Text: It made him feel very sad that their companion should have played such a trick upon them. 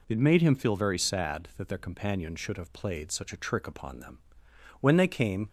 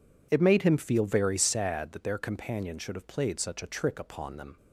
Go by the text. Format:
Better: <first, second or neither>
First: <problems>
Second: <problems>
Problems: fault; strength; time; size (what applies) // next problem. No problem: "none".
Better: second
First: goes on to say "When they came"; noticeable; from 4.8 s on; 0.68 s long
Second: none